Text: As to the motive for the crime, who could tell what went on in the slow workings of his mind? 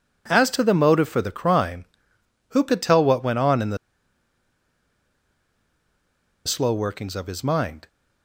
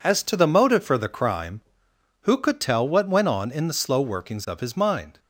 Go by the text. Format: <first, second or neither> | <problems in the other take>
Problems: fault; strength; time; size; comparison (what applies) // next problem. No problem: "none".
second | pauses between "the" and "slow"; strong; at 3.7 s; 2.6 s long